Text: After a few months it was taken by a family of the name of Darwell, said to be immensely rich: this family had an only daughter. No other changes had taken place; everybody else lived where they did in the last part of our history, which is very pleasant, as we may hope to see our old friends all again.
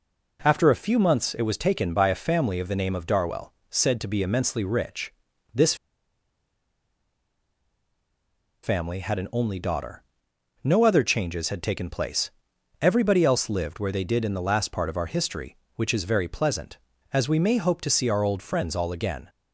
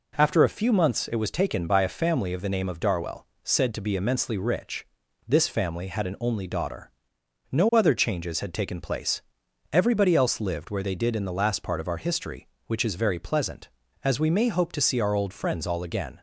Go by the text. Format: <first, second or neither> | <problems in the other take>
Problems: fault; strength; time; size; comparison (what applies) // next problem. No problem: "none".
second | pauses between "this" and "family"; strong; at 5.7 s; 2.8 s long